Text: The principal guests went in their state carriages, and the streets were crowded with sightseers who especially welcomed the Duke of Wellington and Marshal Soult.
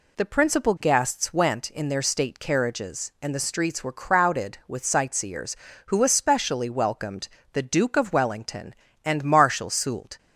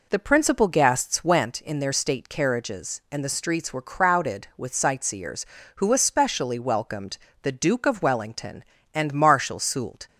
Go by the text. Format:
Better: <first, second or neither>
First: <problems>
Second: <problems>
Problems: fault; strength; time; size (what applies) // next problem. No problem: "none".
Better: first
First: pauses between "welcomed" and "the"; slight; at 7.2 s; 0.24 s long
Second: starts louder than the rest; noticeable; until 1.5 s; 4 dB // pauses between "welcomed" and "the"; slight; at 7.1 s; 0.24 s long